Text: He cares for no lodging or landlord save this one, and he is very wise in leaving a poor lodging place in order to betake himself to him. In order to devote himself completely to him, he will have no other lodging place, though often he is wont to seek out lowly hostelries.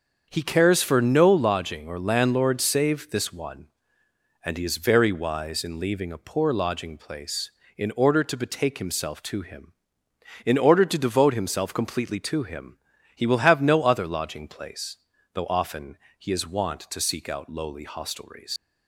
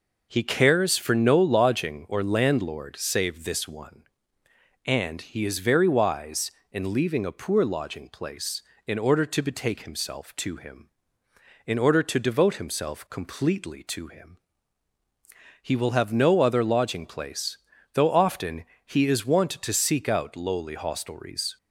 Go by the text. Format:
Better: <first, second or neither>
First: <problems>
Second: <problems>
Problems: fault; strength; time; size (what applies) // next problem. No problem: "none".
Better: second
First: starts louder than the rest; until 1.3 s; 6.5 dB // pauses between "often" and "he"; slight; at 15.9 s; 0.20 s long // leaves "hostelries" unfinished; at 18.5 s; 105 ms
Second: pauses between "often" and "he"; slight; at 18.6 s; 0.20 s long